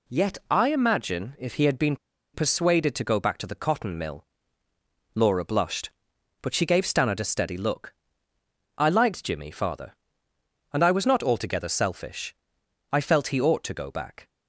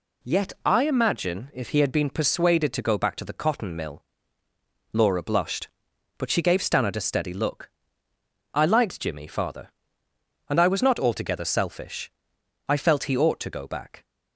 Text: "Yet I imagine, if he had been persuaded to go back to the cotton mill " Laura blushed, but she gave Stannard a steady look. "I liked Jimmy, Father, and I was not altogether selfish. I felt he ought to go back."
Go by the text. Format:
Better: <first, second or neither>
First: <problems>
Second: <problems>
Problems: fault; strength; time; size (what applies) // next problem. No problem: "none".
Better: second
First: pauses between "been" and "persuaded"; at 1.9 s; 0.37 s long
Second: none